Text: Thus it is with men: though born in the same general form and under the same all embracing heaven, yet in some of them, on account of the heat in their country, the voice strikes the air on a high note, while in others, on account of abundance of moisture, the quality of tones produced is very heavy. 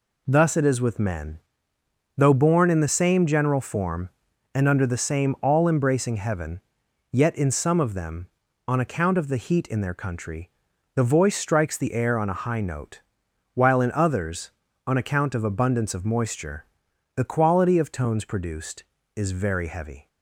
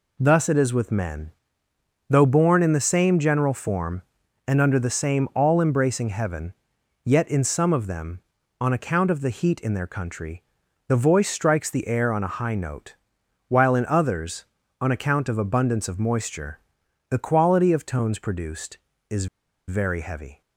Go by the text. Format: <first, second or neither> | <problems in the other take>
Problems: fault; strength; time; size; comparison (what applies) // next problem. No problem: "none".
first | pauses between "is" and "very"; at 19.2 s; 0.42 s long